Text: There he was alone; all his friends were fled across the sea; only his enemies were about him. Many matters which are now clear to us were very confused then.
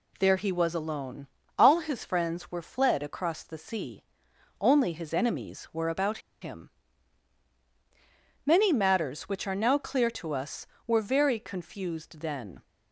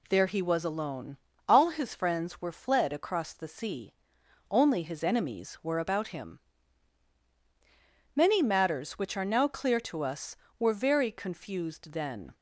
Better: second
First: pauses between "about" and "him"; slight; at 6.1 s; 0.23 s long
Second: none

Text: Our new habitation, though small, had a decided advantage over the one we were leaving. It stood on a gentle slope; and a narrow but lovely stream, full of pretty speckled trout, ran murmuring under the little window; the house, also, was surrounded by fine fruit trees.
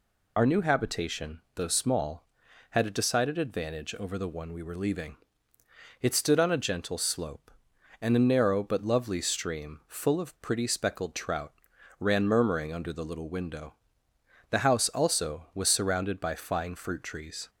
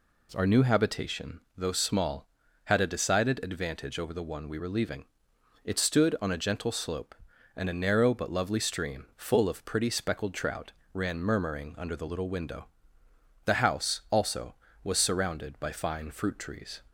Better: second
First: loses the start of "Our"; at 0.3 s; 25 ms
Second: none

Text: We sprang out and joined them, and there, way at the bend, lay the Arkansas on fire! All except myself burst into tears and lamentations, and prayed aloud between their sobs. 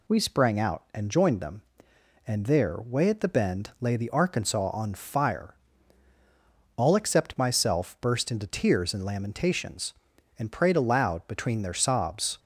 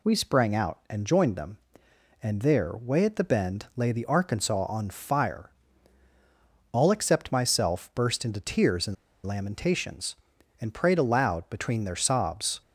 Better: first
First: none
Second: pauses between "and" and "lamentations"; slight; at 8.9 s; 0.29 s long

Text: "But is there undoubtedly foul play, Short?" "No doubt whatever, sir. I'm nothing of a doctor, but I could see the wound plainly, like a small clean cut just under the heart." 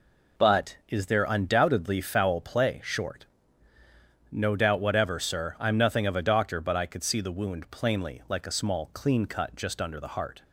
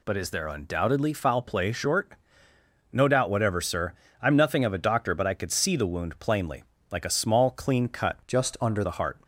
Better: first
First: none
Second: changes voice from "just" to "under"; from 8.2 to 8.8 s; 0.6 s long

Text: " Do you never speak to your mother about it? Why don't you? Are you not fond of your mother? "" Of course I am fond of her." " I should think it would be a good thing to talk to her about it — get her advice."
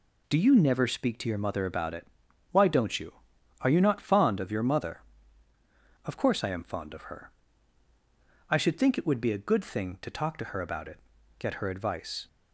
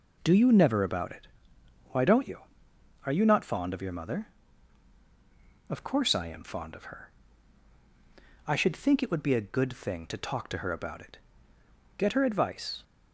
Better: first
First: none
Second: skips "speak to your mother"; at 0.8 s

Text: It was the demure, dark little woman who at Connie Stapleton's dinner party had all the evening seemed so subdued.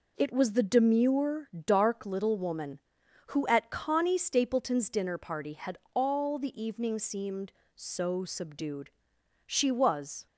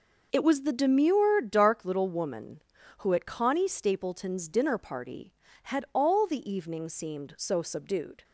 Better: second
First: pauses between "had" and "all"; slight; at 5.7 s; 0.18 s long // goes on to say "She was"; noticeable; from 9.4 s on; 0.80 s long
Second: none

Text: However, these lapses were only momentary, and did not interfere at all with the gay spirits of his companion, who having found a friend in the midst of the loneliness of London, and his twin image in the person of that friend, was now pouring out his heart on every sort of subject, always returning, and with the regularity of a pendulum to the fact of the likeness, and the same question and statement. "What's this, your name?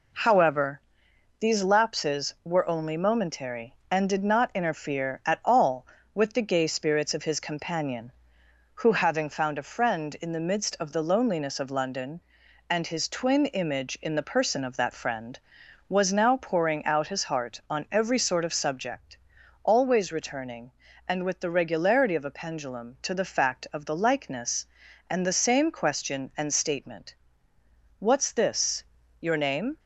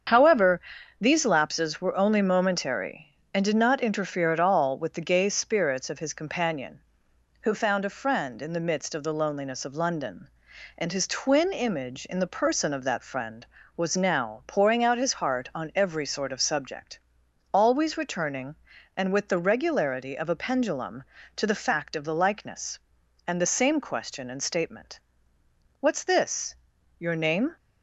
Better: first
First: none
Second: starts louder than the rest; strong; until 1.4 s; 7 dB // skips "having"; at 7.5 s

